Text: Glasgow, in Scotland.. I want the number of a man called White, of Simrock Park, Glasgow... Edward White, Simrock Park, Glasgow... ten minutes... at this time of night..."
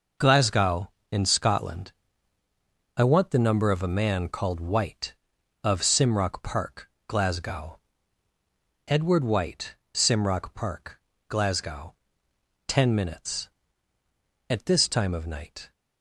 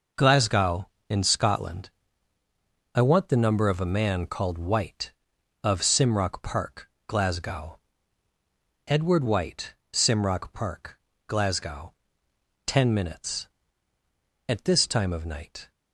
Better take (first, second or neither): neither